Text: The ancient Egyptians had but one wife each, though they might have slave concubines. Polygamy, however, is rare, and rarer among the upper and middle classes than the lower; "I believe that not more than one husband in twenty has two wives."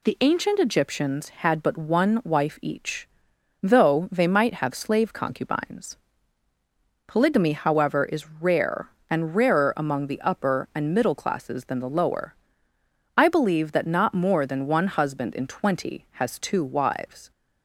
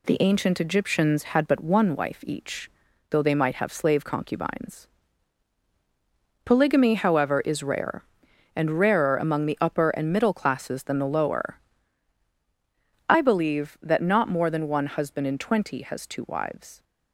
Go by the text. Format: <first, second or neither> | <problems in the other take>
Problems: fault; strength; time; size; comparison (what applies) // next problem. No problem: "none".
neither | none